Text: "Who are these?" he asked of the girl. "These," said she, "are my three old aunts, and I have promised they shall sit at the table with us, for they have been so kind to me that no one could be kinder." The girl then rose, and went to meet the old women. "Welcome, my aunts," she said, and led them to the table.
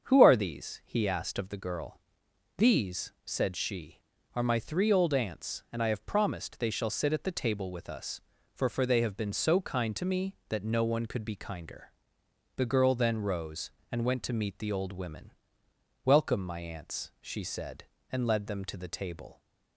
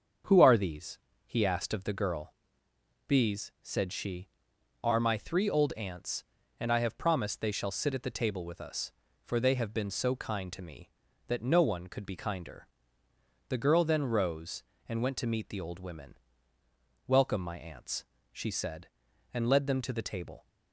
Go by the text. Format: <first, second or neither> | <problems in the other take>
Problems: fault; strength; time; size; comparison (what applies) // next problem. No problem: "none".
second | starts louder than the rest; until 1.0 s; 7 dB; also in the second // says "for" twice; at 8.6 s